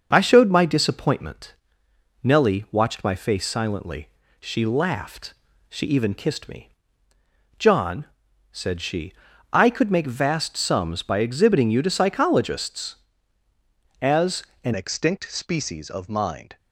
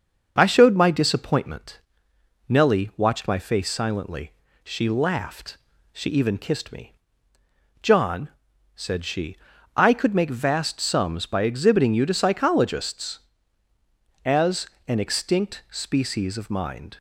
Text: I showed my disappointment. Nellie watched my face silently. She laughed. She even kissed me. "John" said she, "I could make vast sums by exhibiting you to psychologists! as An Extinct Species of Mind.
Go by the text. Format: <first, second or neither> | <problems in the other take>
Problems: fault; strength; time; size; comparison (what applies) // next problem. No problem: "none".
second | starts louder than the rest; until 1.1 s; 6.5 dB; also in the second // pauses between "John" and "said"; noticeable; at 8.0 s; 0.48 s long; noticeable in the second // pauses between "as" and "An"; slight; at 14.4 s; 0.22 s long; slight in the second // changes voice at "Extinct"; from 14.7 s on; 1.8 s long